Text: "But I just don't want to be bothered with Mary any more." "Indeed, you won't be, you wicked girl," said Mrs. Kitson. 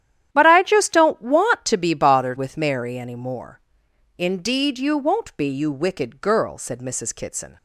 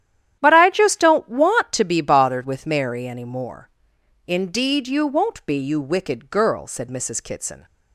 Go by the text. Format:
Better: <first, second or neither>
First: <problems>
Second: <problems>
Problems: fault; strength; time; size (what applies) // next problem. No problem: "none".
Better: neither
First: starts louder than the rest; strong; until 1.3 s; 11 dB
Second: starts louder than the rest; strong; until 1.4 s; 11 dB